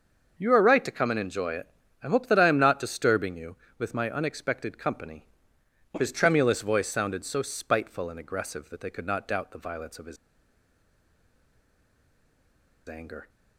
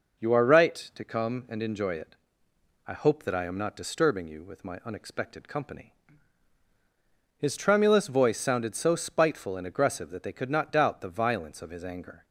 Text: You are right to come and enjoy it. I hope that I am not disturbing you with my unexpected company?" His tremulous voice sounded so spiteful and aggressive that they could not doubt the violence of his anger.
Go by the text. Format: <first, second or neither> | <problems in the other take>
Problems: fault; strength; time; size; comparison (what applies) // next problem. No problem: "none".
second | starts louder than the rest; until 1.3 s; 6.5 dB // pauses between "his" and "anger"; strong; at 10.1 s; 2.7 s long